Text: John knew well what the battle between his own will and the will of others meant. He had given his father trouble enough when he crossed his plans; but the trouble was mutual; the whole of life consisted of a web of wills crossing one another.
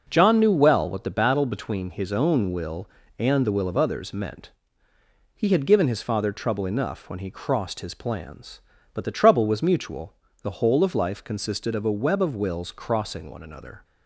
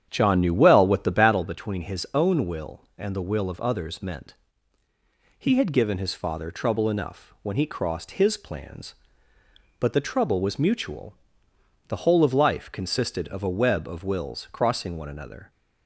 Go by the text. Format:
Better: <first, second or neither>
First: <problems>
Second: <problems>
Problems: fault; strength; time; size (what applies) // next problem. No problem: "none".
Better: first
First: none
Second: starts louder than the rest; strong; until 1.4 s; 9 dB